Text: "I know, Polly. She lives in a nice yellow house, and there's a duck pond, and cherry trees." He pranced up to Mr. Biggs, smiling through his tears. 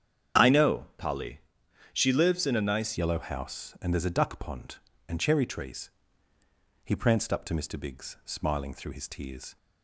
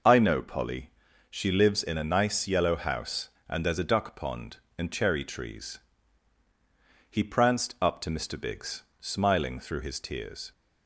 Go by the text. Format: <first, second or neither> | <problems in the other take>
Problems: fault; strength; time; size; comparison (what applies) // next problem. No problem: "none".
second | starts louder than the rest; strong; until 2.0 s; 8 dB // changes voice at "yellow"; from 2.9 s on; 6.6 s long